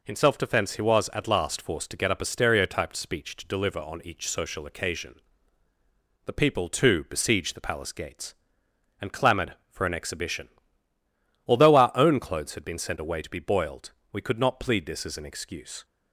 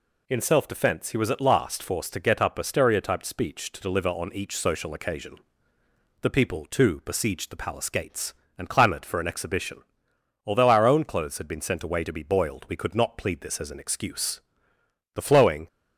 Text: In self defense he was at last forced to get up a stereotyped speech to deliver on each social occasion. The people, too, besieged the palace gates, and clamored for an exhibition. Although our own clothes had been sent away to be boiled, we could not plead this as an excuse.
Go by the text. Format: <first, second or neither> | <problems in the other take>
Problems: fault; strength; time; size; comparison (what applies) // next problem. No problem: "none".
first | goes on to say "The flowing"; from 15.1 s on; 0.52 s long